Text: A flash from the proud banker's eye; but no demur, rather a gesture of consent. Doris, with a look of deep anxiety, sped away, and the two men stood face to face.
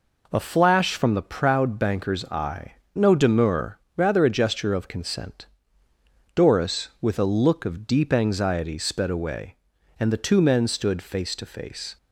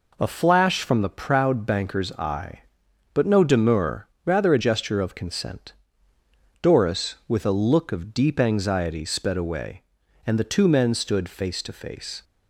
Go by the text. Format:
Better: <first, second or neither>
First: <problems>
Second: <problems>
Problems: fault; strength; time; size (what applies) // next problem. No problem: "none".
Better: second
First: skips "but"; at 2.8 s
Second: none